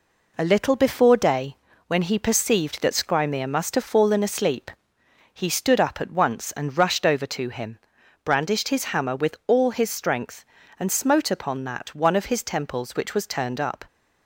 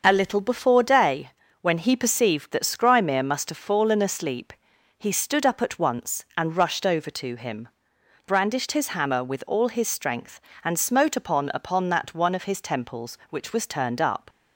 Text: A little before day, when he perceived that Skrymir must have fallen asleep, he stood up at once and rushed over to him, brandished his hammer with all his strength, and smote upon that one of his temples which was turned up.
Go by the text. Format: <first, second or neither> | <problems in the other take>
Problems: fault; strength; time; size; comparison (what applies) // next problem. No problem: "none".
first | starts louder than the rest; until 1.0 s; 6 dB // says "upon" twice; at 11.5 s